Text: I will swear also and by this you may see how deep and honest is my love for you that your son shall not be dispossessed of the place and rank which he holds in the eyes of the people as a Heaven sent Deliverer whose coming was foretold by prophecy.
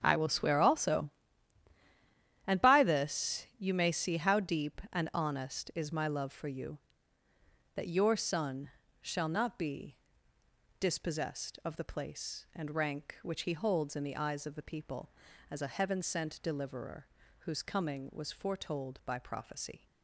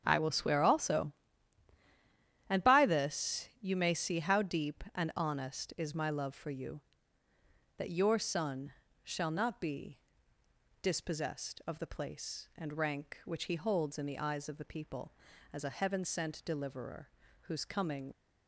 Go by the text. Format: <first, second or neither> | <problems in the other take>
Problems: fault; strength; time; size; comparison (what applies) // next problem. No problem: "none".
first | starts louder than the rest; strong; until 1.0 s; 8 dB; strong in the first // pauses between "son" and "shall"; slight; at 8.7 s; 0.30 s long; slight in the first // pauses between "be" and "dispossessed"; noticeable; at 9.9 s; 0.86 s long; noticeable in the first // pauses between "Deliverer" and "whose"; slight; at 17.0 s; 0.34 s long; slight in the first // stops before "was foretold by prophecy"; at 18.1 s